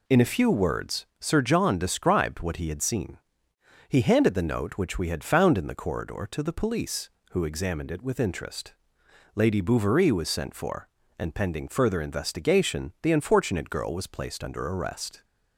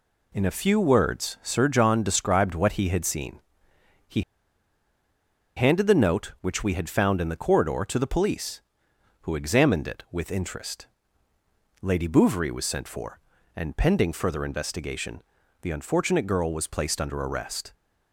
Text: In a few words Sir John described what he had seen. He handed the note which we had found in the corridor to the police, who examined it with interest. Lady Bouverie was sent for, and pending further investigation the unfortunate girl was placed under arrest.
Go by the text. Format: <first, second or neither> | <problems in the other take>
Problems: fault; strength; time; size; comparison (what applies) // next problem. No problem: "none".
first | pauses between "He" and "handed"; strong; at 4.2 s; 1.3 s long // pauses between "investigation" and "the"; at 15.2 s; 0.42 s long